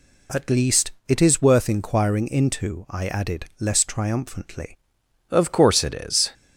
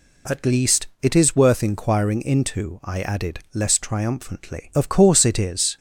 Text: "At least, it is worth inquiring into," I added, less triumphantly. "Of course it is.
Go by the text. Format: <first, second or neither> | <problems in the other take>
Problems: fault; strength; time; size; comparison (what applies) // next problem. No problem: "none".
second | changes voice at "Of"; from 5.2 s on; 1.1 s long